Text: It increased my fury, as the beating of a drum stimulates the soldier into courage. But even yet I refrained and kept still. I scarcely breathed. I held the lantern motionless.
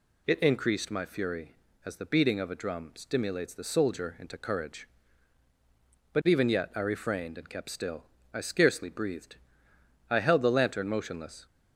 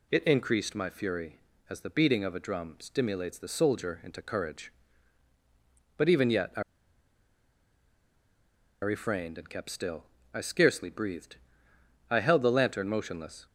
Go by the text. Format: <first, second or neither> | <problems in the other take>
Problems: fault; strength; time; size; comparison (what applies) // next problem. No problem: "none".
first | pauses between "I" and "refrained"; strong; at 6.6 s; 2.2 s long